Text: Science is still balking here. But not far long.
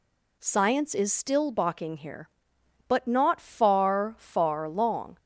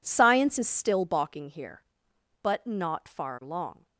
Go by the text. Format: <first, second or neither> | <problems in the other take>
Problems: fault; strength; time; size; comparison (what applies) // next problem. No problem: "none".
second | says "far" twice; at 4.1 s